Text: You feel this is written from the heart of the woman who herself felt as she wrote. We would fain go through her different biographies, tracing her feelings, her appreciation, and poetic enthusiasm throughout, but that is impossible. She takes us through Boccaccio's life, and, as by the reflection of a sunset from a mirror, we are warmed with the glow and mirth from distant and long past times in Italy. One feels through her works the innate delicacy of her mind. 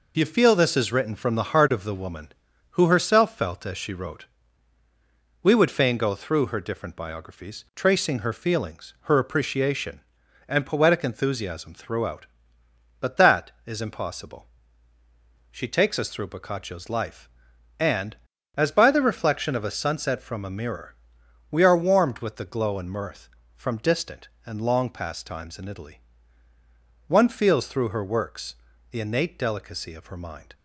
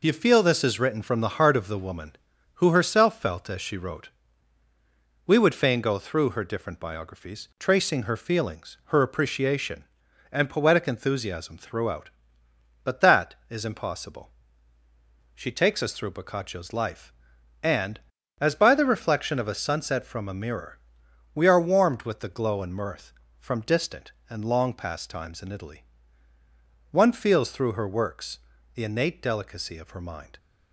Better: neither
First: pauses between "works" and "the"; slight; at 28.5 s; 0.34 s long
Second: pauses between "works" and "the"; slight; at 28.3 s; 0.34 s long

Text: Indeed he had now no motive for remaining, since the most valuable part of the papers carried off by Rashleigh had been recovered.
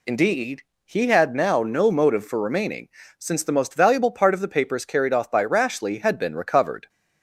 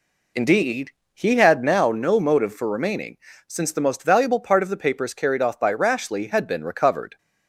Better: first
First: pauses between "Indeed" and "he"; slight; at 0.6 s; 0.22 s long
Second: starts louder than the rest; slight; until 2.0 s; 3 dB // pauses between "Indeed" and "he"; slight; at 0.9 s; 0.22 s long

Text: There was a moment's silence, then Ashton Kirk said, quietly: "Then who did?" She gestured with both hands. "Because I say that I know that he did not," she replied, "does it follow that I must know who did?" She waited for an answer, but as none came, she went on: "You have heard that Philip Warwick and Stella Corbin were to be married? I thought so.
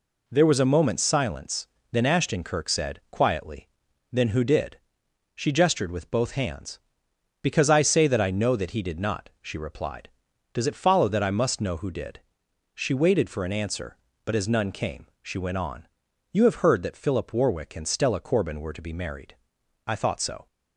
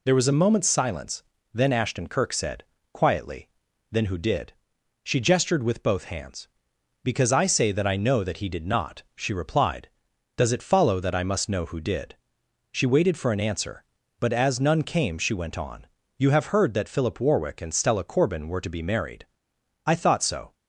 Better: neither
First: none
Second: none

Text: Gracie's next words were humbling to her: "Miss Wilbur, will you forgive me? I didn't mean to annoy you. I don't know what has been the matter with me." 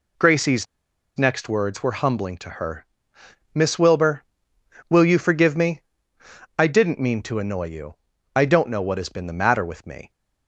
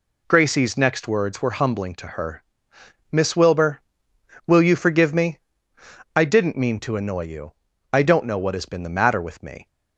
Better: second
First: pauses between "Gracie's" and "next"; noticeable; at 0.6 s; 0.50 s long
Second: none

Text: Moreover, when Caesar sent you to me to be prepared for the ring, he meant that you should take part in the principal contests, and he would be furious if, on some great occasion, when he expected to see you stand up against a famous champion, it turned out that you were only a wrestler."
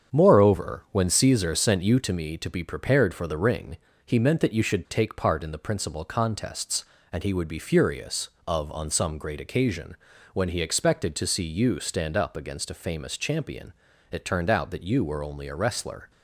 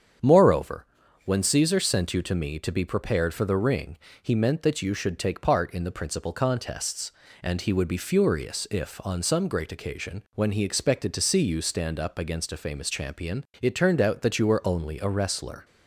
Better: second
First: starts louder than the rest; strong; until 1.2 s; 7.5 dB // says "of" for "if"; at 8.4 s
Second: starts louder than the rest; strong; until 1.6 s; 8 dB

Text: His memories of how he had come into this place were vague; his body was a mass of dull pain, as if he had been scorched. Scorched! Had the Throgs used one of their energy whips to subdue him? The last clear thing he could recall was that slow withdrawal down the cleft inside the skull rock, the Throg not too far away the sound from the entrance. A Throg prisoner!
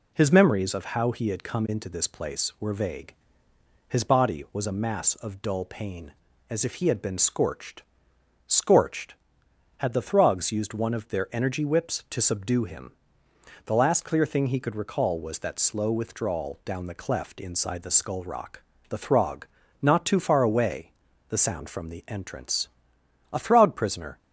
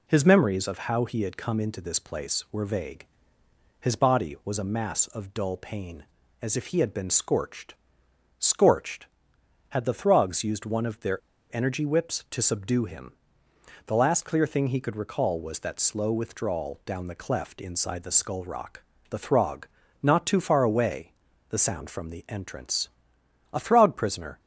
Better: first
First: pauses between "Throg" and "not"; slight; at 19.4 s; 0.36 s long // pauses between "away" and "the"; slight; at 20.9 s; 0.36 s long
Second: pauses between "their" and "energy"; slight; at 11.1 s; 0.32 s long // pauses between "Throg" and "not"; slight; at 19.6 s; 0.36 s long // pauses between "away" and "the"; slight; at 21.1 s; 0.36 s long

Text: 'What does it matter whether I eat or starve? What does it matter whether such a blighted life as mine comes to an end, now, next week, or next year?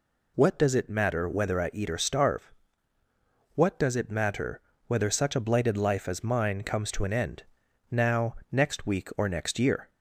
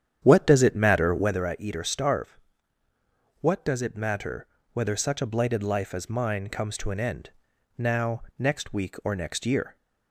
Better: first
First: pauses between "matter" and "whether"; slight; at 4.5 s; 0.28 s long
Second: starts louder than the rest; strong; until 1.4 s; 9 dB // pauses between "matter" and "whether"; slight; at 4.4 s; 0.28 s long

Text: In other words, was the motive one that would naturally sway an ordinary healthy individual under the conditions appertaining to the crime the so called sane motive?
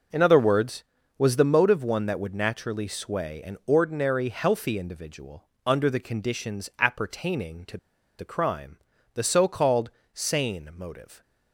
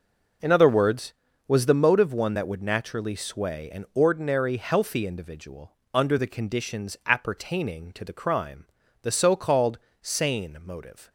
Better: second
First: pauses between "individual" and "under"; slight; at 5.4 s; 0.20 s long // pauses between "to" and "the"; at 7.7 s; 0.42 s long // pauses between "crime" and "the"; slight; at 8.7 s; 0.36 s long // pauses between "called" and "sane"; slight; at 9.8 s; 0.24 s long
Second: pauses between "individual" and "under"; slight; at 5.7 s; 0.20 s long // pauses between "crime" and "the"; slight; at 8.6 s; 0.36 s long // pauses between "called" and "sane"; slight; at 9.7 s; 0.24 s long

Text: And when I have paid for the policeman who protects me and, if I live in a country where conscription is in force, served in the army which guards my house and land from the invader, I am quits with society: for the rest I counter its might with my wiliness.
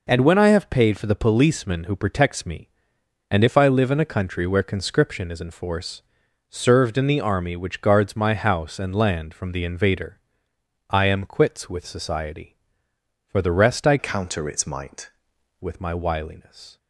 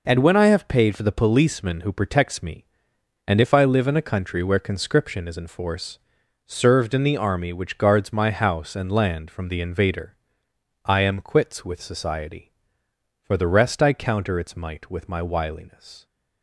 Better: second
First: changes voice from "counter" to "might"; from 13.9 to 15.0 s; 1.1 s long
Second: none

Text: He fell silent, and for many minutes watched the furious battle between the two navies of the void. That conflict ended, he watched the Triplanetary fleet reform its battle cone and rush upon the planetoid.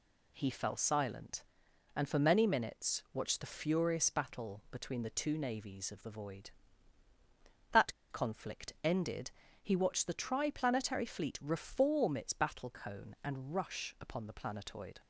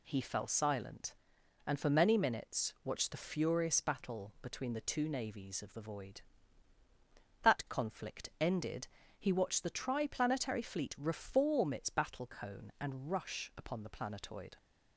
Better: second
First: pauses between "That" and "conflict"; slight; at 7.9 s; 0.19 s long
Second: none

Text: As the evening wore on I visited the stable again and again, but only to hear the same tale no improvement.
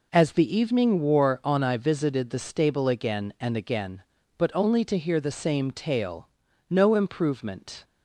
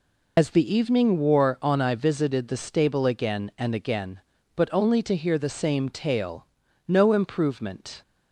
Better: first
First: pauses between "tale" and "no"; at 6.2 s; 0.40 s long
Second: loses the start of "As"; at 0.3 s; 75 ms // pauses between "tale" and "no"; at 6.4 s; 0.40 s long

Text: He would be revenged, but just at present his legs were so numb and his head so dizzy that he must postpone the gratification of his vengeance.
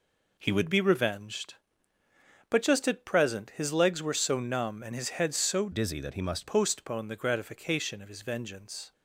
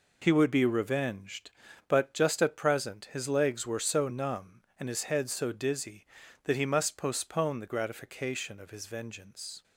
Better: second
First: changes voice from "dizzy" to "must"; from 5.7 to 6.4 s; 0.7 s long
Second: none

